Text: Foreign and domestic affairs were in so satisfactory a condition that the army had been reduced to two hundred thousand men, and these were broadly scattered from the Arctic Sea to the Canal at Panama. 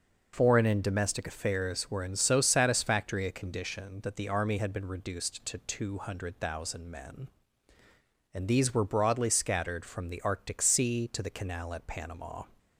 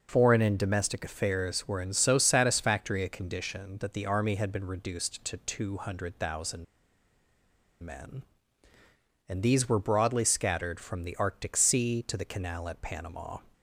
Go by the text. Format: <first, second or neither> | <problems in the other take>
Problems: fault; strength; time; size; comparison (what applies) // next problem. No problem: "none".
first | pauses between "thousand" and "men"; at 6.6 s; 1.1 s long